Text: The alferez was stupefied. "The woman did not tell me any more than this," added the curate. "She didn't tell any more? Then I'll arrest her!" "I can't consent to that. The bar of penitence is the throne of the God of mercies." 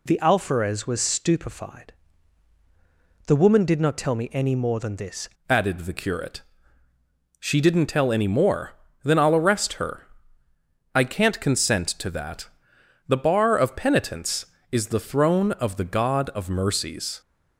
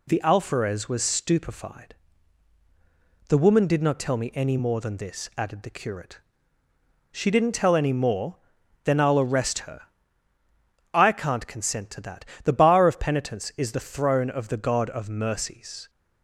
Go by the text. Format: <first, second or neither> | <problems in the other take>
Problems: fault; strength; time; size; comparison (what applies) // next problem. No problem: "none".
second | changes voice at "added"; from 5.4 s on; 11.8 s long